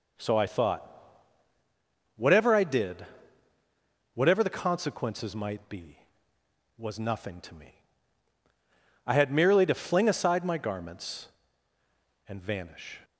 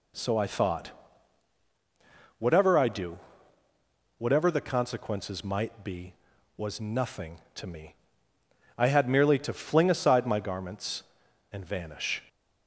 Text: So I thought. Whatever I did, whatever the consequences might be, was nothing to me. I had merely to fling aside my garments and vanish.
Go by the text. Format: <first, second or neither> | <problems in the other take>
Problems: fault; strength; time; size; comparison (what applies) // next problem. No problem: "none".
first | says "do" for "did"; at 2.8 s